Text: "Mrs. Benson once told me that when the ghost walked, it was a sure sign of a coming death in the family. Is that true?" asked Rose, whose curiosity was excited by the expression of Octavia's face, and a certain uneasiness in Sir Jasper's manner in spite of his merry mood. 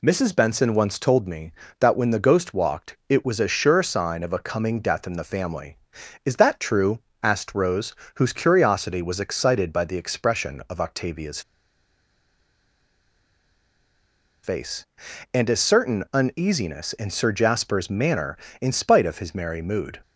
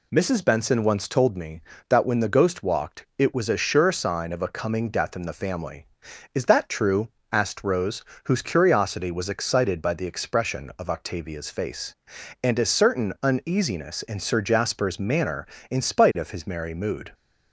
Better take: second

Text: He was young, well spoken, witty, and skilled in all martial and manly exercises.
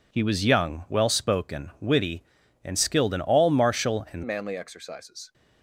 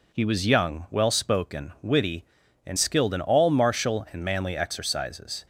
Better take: second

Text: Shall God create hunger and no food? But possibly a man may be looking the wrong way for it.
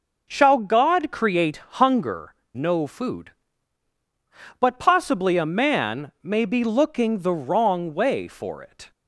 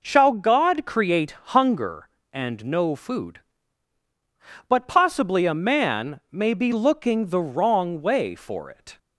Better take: second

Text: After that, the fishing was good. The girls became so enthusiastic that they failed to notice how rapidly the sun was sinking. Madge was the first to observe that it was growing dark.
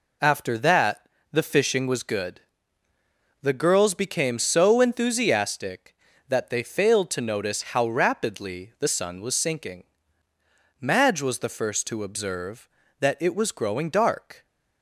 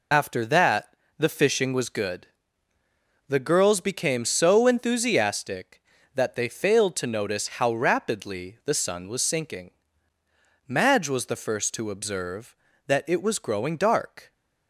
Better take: first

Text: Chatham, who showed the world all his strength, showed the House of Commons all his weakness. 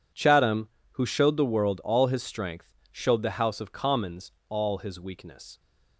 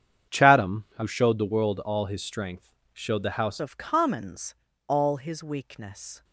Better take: first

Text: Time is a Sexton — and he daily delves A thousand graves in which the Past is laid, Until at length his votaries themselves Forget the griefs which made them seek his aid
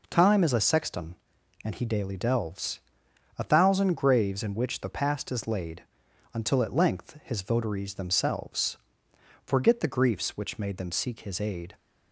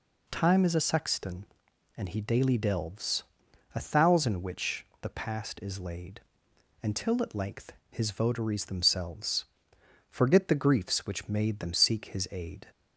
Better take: first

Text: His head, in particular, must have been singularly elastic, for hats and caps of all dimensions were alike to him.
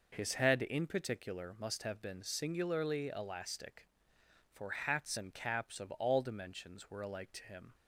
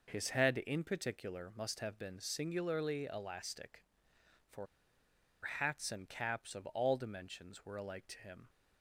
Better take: first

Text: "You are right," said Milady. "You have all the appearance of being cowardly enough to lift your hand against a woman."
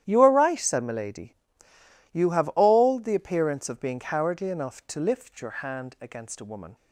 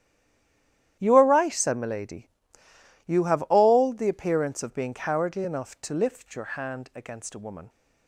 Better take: first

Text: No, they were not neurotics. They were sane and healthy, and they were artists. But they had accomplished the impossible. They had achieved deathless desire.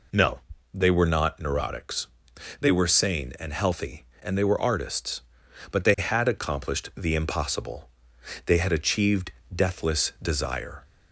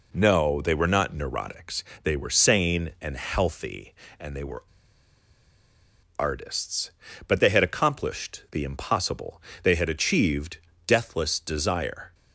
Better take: first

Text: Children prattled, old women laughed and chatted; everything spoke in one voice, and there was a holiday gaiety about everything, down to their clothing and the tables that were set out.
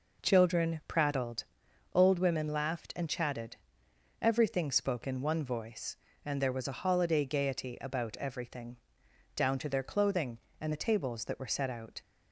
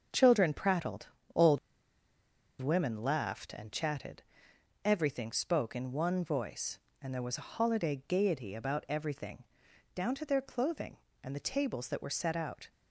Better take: first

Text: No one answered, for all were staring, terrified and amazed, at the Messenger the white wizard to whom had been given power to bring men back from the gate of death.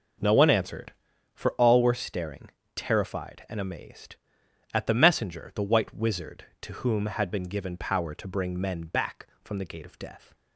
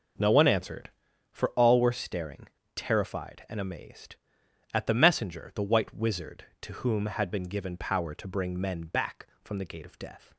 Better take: neither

